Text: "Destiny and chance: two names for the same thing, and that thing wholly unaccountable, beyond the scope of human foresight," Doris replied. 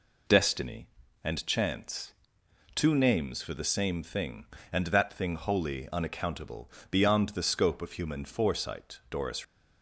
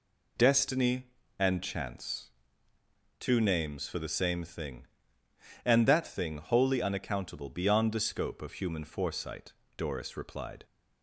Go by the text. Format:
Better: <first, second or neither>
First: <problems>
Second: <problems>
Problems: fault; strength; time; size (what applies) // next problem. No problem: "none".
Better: second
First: stops before "replied"; at 9.4 s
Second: none